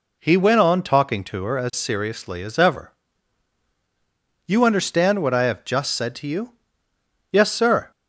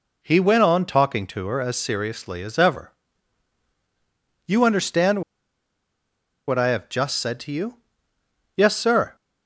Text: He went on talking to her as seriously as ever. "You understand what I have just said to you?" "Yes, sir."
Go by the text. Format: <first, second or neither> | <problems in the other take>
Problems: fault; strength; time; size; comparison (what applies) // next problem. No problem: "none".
first | pauses between "understand" and "what"; strong; at 5.2 s; 1.2 s long